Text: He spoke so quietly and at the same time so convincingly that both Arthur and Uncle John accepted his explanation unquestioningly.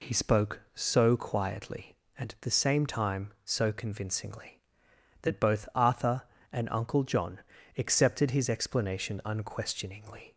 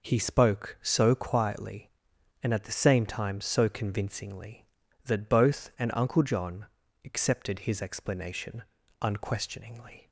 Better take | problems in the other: first | skips "Arthur"; at 5.7 s // pauses between "John" and "accepted"; at 6.6 s; 0.38 s long; also in the first // pauses between "explanation" and "unquestioningly"; slight; at 8.6 s; 0.36 s long

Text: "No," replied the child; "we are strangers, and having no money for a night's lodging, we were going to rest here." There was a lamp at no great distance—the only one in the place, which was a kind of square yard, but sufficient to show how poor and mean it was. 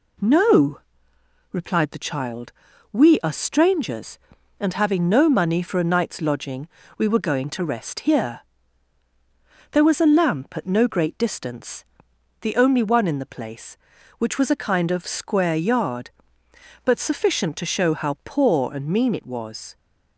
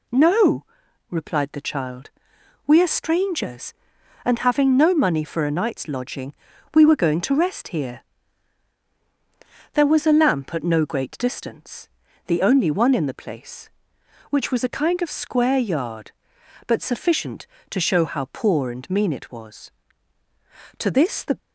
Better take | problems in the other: first | goes on to say "To this the"; from 20.7 s on; 0.60 s long

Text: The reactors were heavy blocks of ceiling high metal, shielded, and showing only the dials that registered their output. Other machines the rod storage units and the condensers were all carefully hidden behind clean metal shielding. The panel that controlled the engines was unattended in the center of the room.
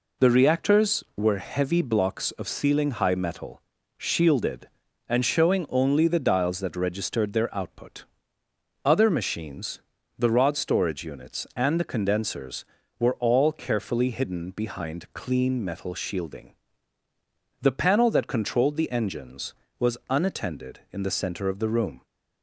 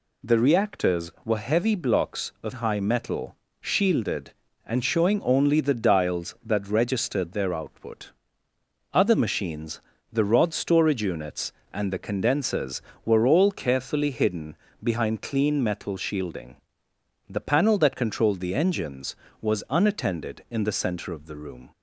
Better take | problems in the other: first | skips "ceiling"; at 2.5 s // pauses between "machines" and "the"; slight; at 9.8 s; 0.30 s long; slight in the first // pauses between "hidden" and "behind"; slight; at 14.5 s; 0.26 s long

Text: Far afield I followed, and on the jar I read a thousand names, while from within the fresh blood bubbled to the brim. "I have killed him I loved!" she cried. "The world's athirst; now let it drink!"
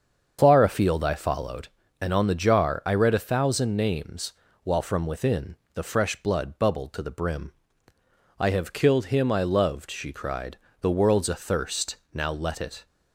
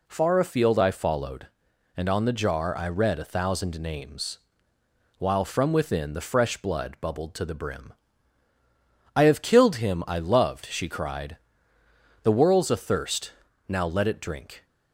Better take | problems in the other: second | starts louder than the rest; until 1.4 s; 7 dB // pauses between "within" and "the"; slight; at 5.5 s; 0.18 s long // stops before "drink"; at 12.8 s

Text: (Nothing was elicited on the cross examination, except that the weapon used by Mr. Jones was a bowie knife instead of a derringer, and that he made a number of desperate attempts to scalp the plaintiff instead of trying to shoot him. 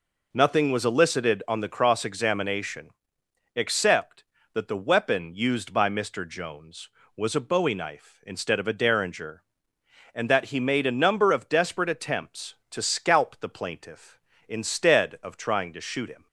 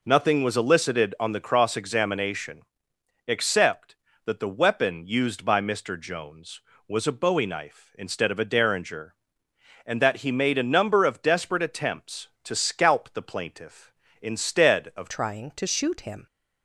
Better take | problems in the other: first | changes voice at "trying"; from 15.0 s on; 1.2 s long

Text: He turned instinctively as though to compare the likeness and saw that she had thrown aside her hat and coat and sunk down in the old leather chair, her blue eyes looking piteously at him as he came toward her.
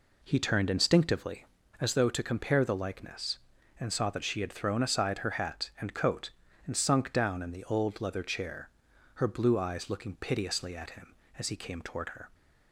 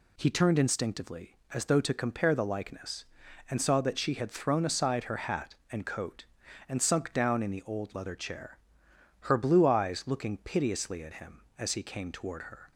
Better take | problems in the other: second | starts louder than the rest; slight; until 1.7 s; 3.5 dB

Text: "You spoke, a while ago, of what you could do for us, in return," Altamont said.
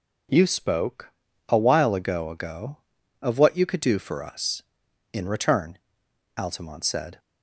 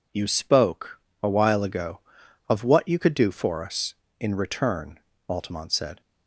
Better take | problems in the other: second | says "ago" twice; at 2.2 s

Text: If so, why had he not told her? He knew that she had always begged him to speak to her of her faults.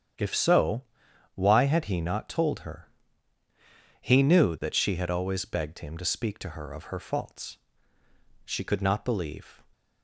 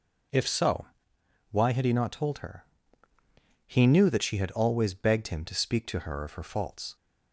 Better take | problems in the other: second | starts louder than the rest; strong; until 1.7 s; 9 dB // goes on to say "She could not believe"; noticeable; from 8.4 s on; 1.1 s long

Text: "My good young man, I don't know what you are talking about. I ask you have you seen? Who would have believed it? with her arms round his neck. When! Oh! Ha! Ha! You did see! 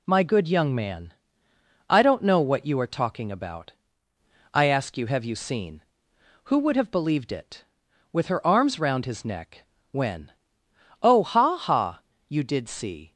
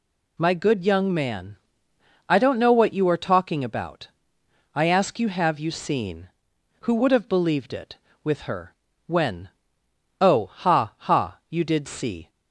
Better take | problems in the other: first | skips "arms round his neck"; at 8.9 s

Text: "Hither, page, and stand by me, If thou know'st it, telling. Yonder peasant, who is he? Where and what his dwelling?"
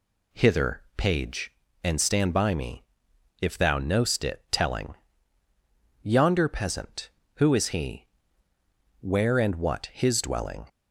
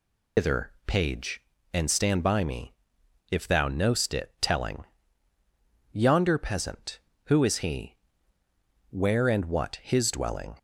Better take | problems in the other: first | loses the start of "Hither"; at 0.3 s; 145 ms

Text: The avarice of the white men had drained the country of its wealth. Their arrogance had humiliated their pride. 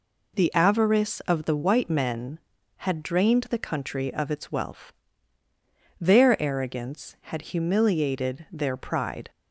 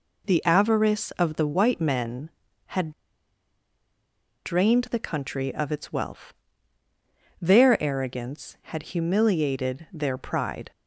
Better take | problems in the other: first | pauses between "had" and "drained"; strong; at 2.9 s; 1.5 s long

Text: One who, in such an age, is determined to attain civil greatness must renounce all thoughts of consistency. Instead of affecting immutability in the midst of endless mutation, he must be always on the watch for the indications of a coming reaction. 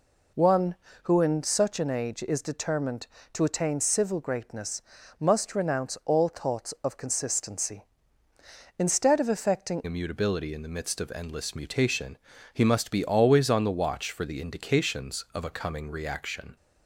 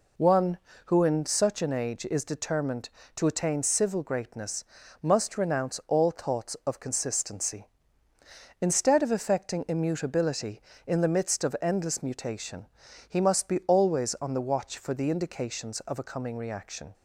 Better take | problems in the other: second | pauses between "greatness" and "must"; at 4.8 s; 0.38 s long; also in the second // changes voice at "immutability"; from 9.8 s on; 6.7 s long

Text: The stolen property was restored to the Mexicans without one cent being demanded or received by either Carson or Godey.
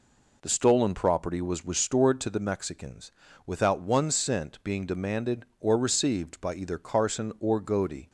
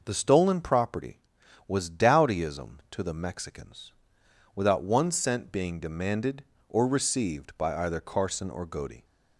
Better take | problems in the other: first | says "dowdyism" for "restored"; at 1.8 s // pauses between "Mexicans" and "without"; noticeable; at 3.9 s; 0.64 s long; slight in the first

